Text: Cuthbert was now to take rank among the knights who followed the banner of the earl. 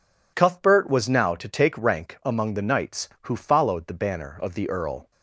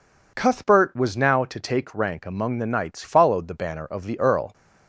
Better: first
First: none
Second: skips "who"; at 3.0 s

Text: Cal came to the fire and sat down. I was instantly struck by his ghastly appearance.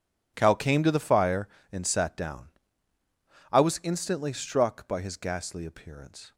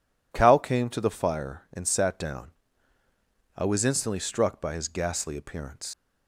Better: first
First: none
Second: leaves "appearance" unfinished; at 5.9 s; 120 ms

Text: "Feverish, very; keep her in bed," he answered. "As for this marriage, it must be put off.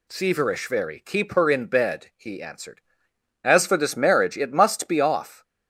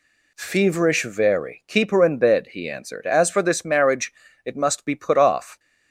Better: second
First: skips "put"; at 5.0 s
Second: none

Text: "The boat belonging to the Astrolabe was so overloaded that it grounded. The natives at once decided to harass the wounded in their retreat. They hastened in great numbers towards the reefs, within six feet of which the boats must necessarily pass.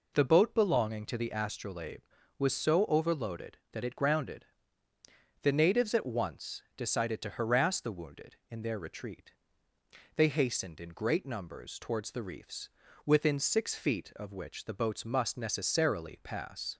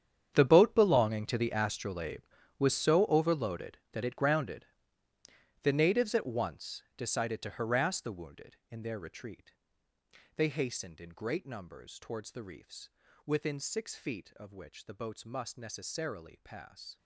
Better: first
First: pauses between "once" and "decided"; slight; at 6.6 s; 0.16 s long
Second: gets quieter; strong; throughout; 16.5 dB // pauses between "once" and "decided"; slight; at 6.8 s; 0.16 s long

